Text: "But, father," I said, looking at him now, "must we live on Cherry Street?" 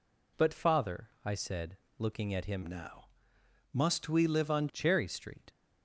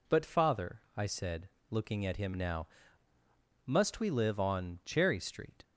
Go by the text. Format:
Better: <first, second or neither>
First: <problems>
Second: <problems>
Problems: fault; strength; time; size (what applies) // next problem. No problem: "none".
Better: second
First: changes voice from "now" to "on"; from 2.6 to 4.6 s; 2.0 s long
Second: none